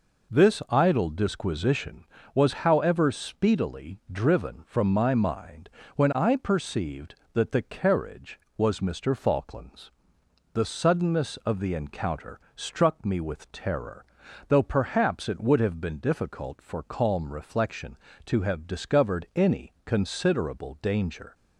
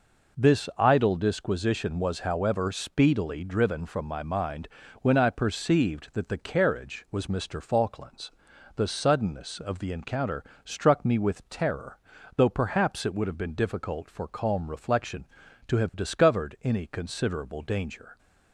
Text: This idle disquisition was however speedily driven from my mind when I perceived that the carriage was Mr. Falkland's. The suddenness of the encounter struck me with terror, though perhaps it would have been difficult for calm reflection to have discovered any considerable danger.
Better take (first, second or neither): neither